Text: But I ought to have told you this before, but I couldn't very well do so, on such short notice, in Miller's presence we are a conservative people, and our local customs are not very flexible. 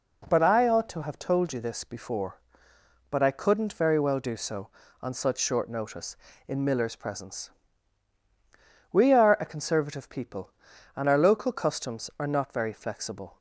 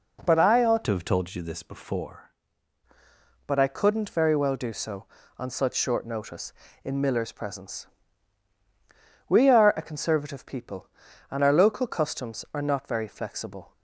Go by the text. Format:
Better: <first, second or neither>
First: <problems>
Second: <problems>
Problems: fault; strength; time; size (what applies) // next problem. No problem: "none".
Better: first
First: pauses between "presence" and "we"; strong; at 7.4 s; 1.4 s long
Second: changes voice from "to" to "before"; from 0.8 to 2.3 s; 1.5 s long // pauses between "presence" and "we"; strong; at 7.8 s; 1.4 s long